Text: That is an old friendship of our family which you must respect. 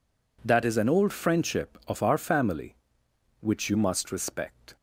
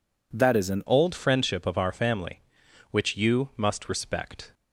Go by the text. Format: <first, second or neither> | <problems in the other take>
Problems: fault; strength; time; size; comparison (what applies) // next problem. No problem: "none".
first | changes voice at "old"; from 0.8 s on; 3.7 s long